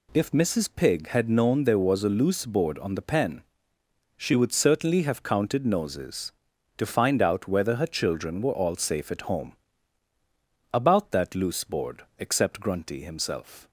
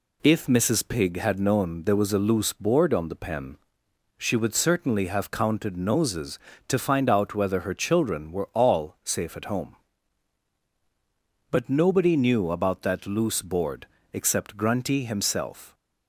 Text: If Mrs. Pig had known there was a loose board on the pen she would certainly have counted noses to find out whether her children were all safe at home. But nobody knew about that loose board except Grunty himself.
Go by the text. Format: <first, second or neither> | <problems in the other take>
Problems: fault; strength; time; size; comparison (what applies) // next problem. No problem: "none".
second | pauses between "pen" and "she"; noticeable; at 3.4 s; 0.74 s long; noticeable in the second // skips "But nobody knew"; at 10.1 s // pauses between "board" and "except"; slight; at 12.0 s; 0.16 s long; slight in the second